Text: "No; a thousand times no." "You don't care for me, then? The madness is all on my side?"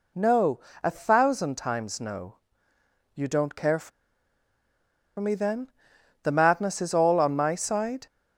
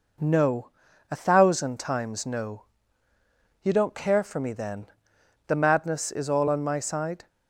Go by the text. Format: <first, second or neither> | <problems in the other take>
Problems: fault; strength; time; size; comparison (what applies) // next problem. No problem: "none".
second | pauses between "for" and "me"; strong; at 3.9 s; 1.2 s long